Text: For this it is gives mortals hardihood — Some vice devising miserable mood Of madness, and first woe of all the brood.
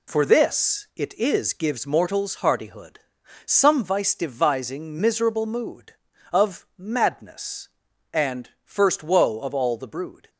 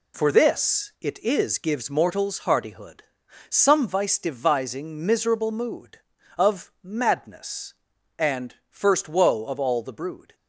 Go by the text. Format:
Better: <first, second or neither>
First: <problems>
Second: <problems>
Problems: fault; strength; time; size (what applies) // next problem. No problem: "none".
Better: neither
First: none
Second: none